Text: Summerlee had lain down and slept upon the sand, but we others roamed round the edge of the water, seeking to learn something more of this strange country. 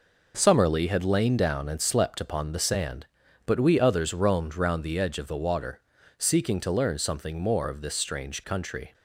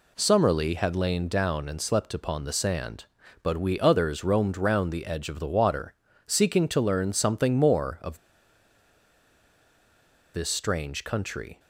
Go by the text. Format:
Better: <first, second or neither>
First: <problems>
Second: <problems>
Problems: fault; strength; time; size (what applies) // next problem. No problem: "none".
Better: first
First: none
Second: pauses between "of" and "this"; strong; at 8.1 s; 2.1 s long